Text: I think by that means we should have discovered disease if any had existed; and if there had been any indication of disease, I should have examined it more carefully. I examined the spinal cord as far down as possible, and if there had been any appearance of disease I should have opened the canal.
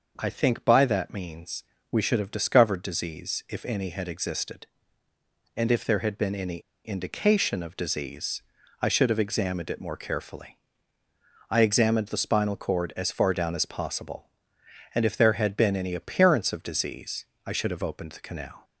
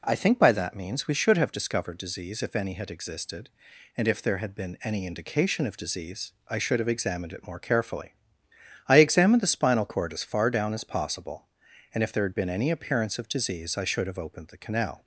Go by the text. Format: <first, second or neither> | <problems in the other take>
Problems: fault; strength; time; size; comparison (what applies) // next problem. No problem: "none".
second | pauses between "means" and "we"; slight; at 1.6 s; 0.28 s long // pauses between "any" and "indication"; slight; at 6.5 s; 0.25 s long // pauses between "disease" and "I"; slight; at 17.2 s; 0.20 s long